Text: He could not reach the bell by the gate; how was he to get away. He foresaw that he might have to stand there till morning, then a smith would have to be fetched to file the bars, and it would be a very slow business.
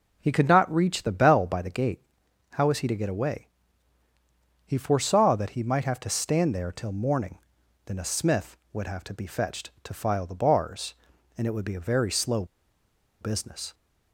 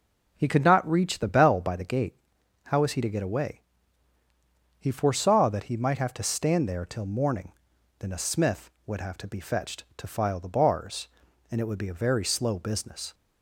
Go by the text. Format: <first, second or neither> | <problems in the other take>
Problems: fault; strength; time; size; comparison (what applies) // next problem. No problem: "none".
second | pauses between "slow" and "business"; noticeable; at 12.4 s; 0.76 s long